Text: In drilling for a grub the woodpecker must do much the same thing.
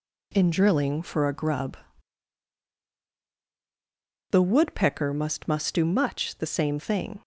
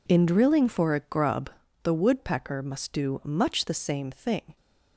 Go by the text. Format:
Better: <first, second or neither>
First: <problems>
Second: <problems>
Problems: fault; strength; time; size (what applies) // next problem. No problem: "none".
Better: second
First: pauses between "grub" and "the"; strong; at 1.7 s; 2.5 s long // says "must" twice; at 5.4 s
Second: pauses between "grub" and "the"; slight; at 1.4 s; 0.32 s long